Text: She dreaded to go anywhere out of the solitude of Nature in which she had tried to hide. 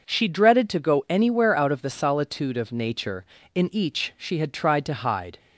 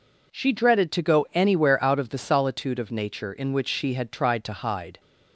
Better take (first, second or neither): second